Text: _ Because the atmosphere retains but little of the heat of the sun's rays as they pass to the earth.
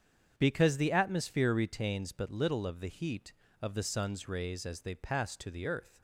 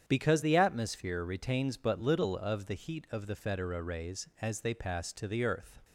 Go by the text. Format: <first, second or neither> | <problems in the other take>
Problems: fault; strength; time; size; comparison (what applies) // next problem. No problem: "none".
first | starts louder than the rest; strong; until 1.0 s; 8.5 dB; strong in the first // says "federa" for "sun's"; at 3.3 s